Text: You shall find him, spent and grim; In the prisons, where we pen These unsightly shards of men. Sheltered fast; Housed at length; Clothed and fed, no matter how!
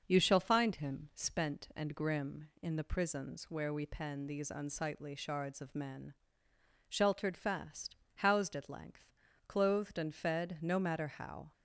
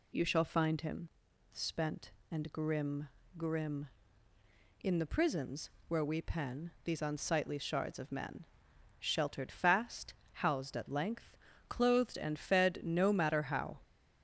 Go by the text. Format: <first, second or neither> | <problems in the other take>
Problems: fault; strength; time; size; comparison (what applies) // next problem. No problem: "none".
first | says "grim" twice; at 3.3 s